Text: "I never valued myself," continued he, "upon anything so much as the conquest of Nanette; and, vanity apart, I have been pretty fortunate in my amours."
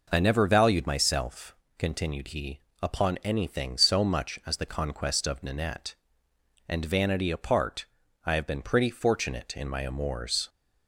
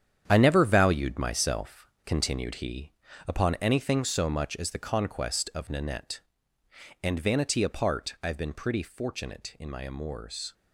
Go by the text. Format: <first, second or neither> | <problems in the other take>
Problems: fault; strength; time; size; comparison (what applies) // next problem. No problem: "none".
first | gets quieter; strong; throughout; 9.5 dB